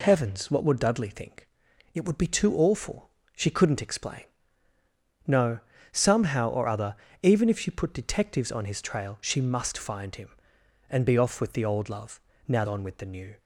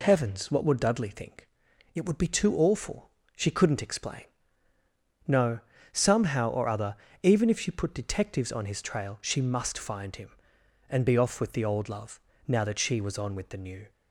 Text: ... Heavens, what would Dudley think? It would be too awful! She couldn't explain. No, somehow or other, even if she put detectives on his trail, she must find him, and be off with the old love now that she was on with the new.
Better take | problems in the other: second | pauses between "love" and "now"; slight; at 12.1 s; 0.28 s long; slight in the second // skips "that she was"; at 12.6 s

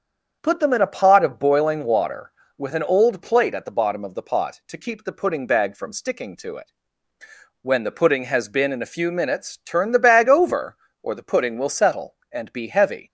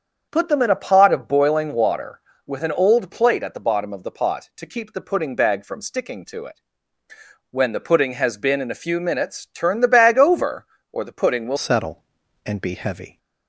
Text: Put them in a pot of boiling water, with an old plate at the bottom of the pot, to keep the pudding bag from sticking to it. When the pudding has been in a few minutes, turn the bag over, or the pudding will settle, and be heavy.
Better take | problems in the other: first | starts louder than the rest; strong; until 1.3 s; 7.5 dB; strong in the first // changes voice at "settle"; from 11.5 s on; 1.6 s long

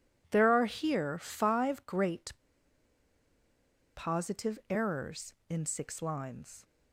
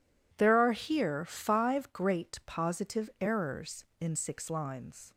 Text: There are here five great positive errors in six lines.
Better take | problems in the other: second | pauses between "great" and "positive"; strong; at 2.3 s; 1.6 s long

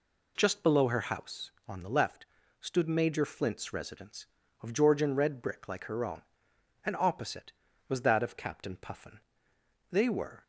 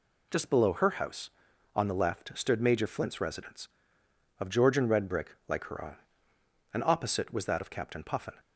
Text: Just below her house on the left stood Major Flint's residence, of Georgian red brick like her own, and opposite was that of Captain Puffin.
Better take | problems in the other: second | pauses between "left" and "stood"; slight; at 2.2 s; 0.34 s long // goes on to say "They were"; from 9.9 s on; 0.52 s long

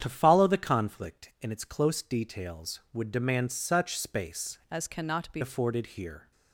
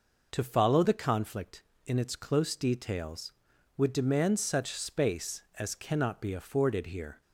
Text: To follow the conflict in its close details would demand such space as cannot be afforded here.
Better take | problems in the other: second | starts louder than the rest; strong; until 1.0 s; 8.5 dB // changes voice from "as" to "be"; from 4.7 to 5.4 s; 0.7 s long

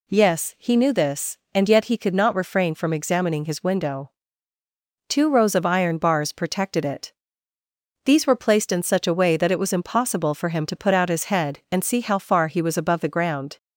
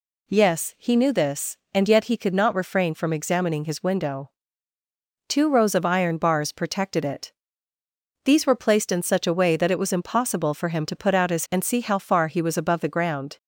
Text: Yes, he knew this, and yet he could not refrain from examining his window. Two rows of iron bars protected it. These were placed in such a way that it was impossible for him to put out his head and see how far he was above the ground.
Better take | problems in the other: first | skips "head"; at 11.4 s

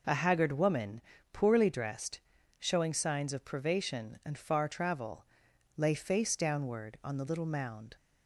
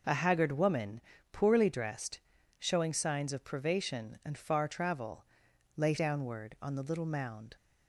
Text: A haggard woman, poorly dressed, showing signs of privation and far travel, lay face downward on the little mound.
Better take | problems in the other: first | skips "face"; at 5.9 s

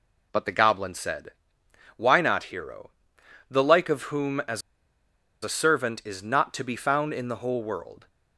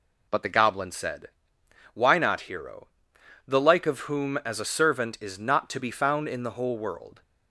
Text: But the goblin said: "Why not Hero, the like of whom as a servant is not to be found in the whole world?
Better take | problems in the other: second | pauses between "as" and "a"; noticeable; at 4.6 s; 0.81 s long

